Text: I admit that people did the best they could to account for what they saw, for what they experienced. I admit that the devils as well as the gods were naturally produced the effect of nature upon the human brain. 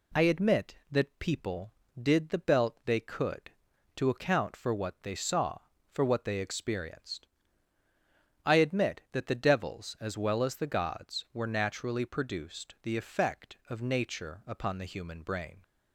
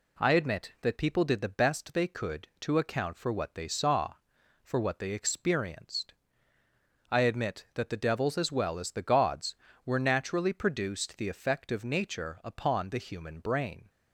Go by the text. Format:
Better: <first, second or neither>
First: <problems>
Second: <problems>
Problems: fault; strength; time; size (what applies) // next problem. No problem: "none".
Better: second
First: says "belt" for "best"; at 2.3 s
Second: none